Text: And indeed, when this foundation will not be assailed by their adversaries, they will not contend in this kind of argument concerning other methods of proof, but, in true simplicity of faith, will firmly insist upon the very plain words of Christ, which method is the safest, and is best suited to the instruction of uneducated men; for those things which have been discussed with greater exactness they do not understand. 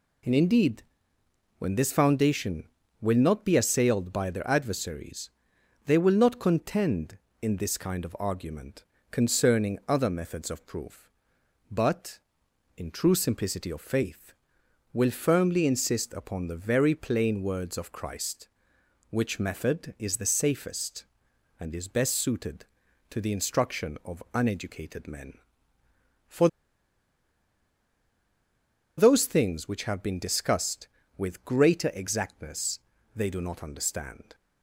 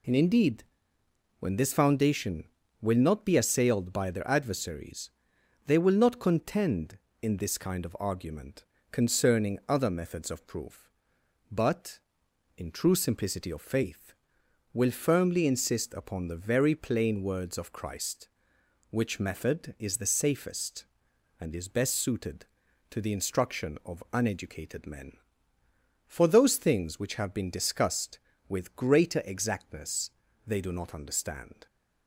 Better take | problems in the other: second | pauses between "argument" and "concerning"; slight; at 8.8 s; 0.26 s long; slight in the second // pauses between "for" and "those"; strong; at 26.4 s; 2.5 s long // pauses between "exactness" and "they"; slight; at 32.7 s; 0.36 s long; slight in the second

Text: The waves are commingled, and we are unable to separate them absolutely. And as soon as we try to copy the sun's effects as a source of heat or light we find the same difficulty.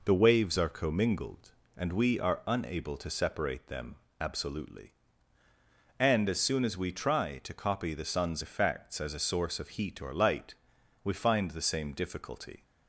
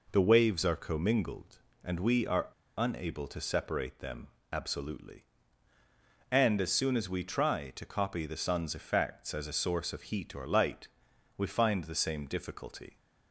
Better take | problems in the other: first | pauses between "are" and "unable"; slight; at 2.4 s; 0.31 s long // pauses between "them" and "absolutely"; slight; at 4.2 s; 0.22 s long; slight in the first // pauses between "light" and "we"; noticeable; at 10.8 s; 0.48 s long; noticeable in the first

